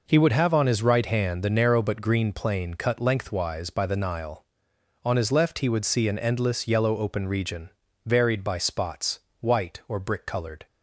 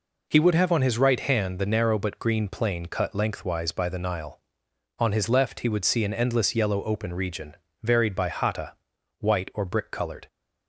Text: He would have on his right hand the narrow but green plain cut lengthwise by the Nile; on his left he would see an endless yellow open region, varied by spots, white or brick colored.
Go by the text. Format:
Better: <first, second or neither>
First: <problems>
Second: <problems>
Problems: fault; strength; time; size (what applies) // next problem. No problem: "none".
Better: first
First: none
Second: says "hata" for "spots"; at 8.2 s